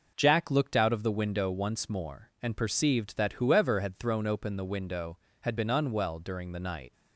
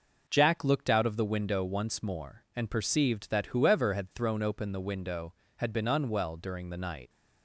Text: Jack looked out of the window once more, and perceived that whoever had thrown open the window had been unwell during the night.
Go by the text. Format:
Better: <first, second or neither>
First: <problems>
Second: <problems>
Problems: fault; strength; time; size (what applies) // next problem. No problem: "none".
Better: neither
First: none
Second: none